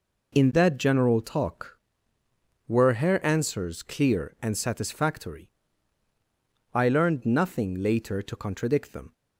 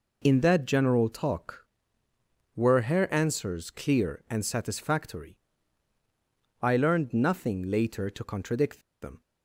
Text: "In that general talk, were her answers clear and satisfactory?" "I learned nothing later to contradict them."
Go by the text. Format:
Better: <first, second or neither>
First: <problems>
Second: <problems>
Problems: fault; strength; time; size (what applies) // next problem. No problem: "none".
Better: first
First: none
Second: pauses between "contradict" and "them"; slight; at 8.7 s; 0.23 s long